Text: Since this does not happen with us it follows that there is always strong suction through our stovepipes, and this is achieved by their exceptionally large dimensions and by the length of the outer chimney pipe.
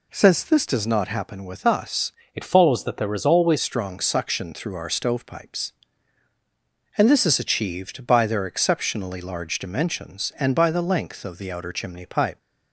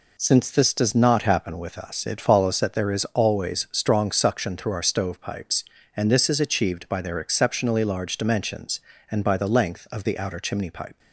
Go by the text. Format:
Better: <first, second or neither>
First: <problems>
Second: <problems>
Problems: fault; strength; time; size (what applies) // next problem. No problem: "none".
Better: second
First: changes voice from "it" to "always"; from 2.3 to 3.5 s; 1.2 s long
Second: none